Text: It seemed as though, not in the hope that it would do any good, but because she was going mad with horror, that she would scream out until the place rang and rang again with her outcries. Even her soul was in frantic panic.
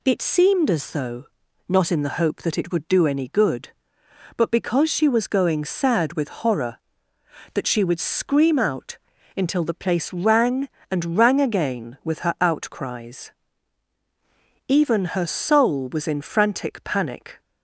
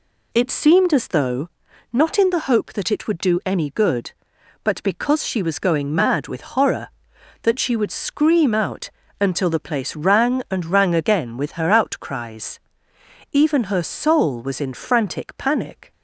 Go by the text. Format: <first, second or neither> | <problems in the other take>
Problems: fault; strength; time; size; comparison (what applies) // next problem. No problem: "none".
second | says "sad" for "mad"; at 5.6 s // pauses between "out" and "until"; at 8.9 s; 0.40 s long; slight in the second